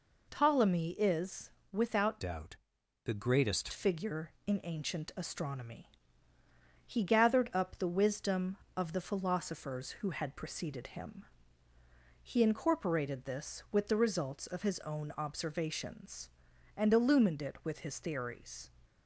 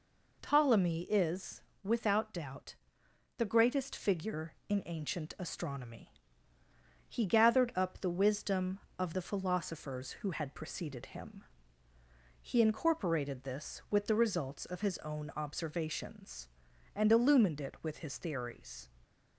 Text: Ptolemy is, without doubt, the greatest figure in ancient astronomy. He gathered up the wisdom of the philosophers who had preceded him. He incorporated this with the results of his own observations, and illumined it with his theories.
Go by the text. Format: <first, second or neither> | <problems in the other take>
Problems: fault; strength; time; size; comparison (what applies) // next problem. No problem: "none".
second | changes voice from "doubt" to "greatest"; from 2.1 to 3.6 s; 1.5 s long